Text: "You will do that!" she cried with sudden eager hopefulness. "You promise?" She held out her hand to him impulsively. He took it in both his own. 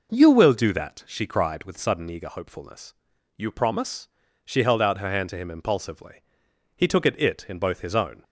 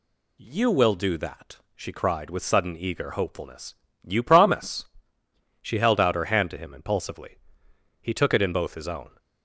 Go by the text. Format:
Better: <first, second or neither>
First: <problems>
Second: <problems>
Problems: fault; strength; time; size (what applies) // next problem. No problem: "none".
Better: second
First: says "it" twice; at 7.2 s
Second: none